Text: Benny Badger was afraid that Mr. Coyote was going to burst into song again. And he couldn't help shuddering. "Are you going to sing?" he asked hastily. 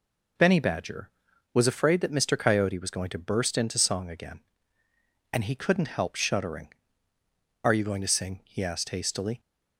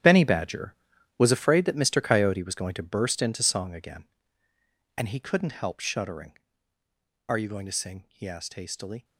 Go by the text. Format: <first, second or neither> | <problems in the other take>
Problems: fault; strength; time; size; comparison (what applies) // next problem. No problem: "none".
first | gets quieter; strong; throughout; 14.5 dB